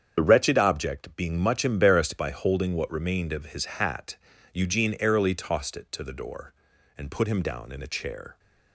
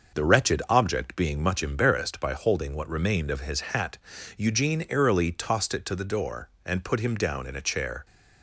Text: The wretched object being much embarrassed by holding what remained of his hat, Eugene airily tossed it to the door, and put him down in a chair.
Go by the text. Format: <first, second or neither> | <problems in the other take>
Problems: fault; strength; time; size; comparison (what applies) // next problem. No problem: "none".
second | loses the start of "The"; at 0.1 s; 50 ms // starts louder than the rest; strong; until 1.2 s; 8 dB; also in the second